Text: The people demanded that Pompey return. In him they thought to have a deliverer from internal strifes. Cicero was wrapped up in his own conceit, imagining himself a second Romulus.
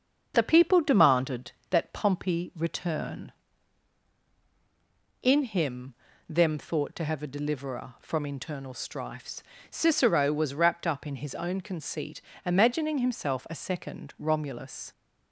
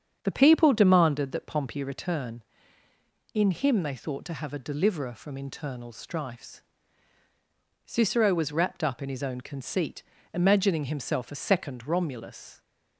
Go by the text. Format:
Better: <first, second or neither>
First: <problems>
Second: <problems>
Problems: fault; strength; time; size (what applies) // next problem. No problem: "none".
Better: second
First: starts louder than the rest; until 1.3 s; 7 dB // says "them" for "they"; at 6.2 s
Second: starts louder than the rest; strong; until 1.2 s; 7.5 dB